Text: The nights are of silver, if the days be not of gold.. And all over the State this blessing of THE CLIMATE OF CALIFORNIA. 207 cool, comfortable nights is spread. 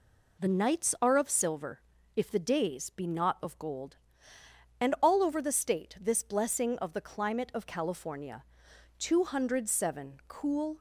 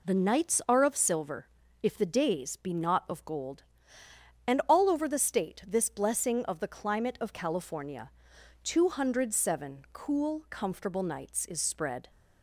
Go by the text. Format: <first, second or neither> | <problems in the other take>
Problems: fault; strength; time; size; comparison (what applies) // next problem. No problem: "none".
second | stops before "comfortable nights is spread"; at 10.7 s